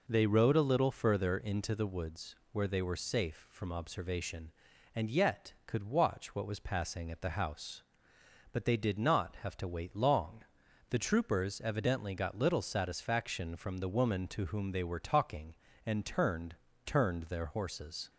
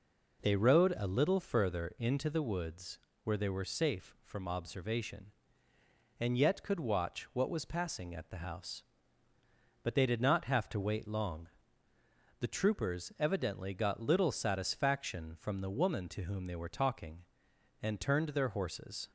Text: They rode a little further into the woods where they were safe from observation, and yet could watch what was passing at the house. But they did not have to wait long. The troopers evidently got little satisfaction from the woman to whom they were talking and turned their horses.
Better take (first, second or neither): second